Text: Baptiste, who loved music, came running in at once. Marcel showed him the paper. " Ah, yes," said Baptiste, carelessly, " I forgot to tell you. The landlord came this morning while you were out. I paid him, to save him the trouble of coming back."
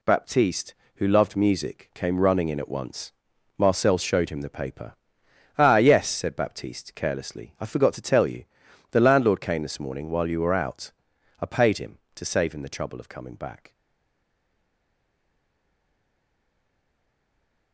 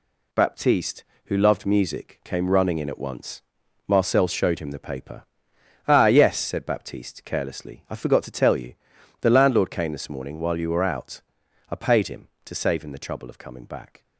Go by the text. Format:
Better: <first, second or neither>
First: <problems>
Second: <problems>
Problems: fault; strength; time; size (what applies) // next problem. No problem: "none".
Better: second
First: stays silent after the last word; strong; from 13.7 s on; 4.0 s long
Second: none